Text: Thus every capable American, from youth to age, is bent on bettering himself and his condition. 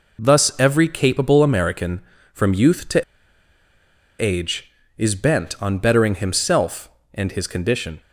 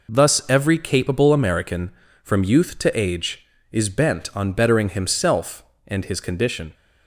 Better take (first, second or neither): second